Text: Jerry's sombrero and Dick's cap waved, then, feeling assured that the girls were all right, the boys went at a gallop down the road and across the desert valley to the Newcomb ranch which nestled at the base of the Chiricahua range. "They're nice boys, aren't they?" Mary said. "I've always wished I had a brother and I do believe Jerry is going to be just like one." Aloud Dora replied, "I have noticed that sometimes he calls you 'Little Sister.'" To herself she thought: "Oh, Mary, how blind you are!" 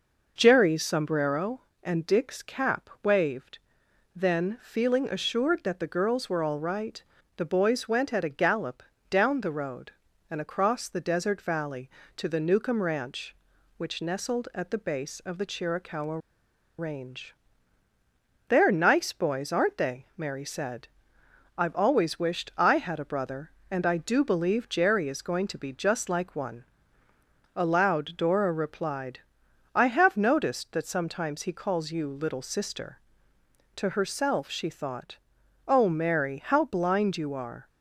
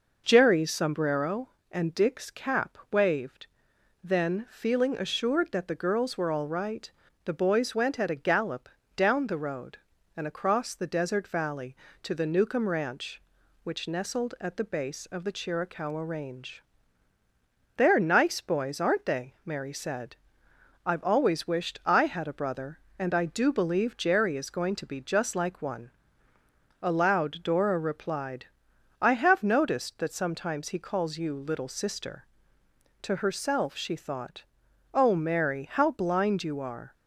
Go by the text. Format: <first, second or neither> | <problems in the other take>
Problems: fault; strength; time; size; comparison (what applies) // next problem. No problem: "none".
second | pauses between "gallop" and "down"; slight; at 8.8 s; 0.28 s long; slight in the second // pauses between "Chiricahua" and "range"; noticeable; at 16.1 s; 0.61 s long